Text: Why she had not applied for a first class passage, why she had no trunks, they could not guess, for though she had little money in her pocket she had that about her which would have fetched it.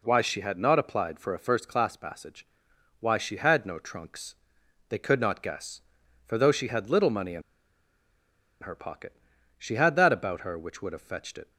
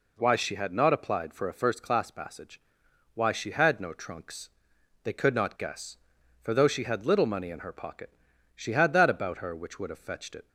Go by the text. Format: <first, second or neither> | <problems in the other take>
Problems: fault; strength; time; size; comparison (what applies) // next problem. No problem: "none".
second | pauses between "in" and "her"; at 7.4 s; 1.2 s long // pauses between "pocket" and "she"; noticeable; at 9.1 s; 0.46 s long; noticeable in the second